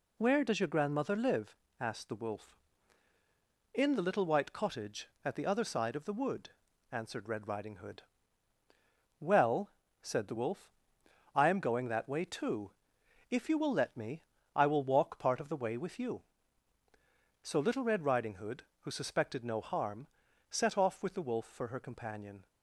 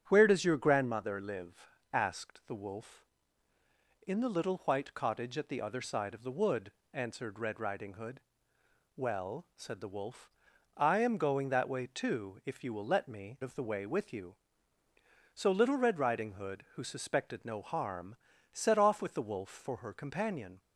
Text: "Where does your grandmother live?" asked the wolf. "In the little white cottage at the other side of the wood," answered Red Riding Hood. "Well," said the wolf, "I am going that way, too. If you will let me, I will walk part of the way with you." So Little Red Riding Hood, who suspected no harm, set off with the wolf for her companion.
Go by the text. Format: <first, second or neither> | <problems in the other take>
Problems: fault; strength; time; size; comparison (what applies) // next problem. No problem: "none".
first | starts louder than the rest; strong; until 1.0 s; 9.5 dB // skips "I will walk part"; at 13.4 s